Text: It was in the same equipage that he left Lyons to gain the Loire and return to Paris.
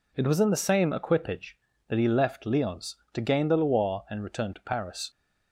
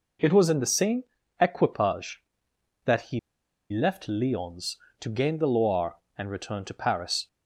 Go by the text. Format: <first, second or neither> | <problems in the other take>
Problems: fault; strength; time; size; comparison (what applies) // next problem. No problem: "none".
first | pauses between "same" and "equipage"; slight; at 1.0 s; 0.36 s long // pauses between "he" and "left"; noticeable; at 3.1 s; 0.53 s long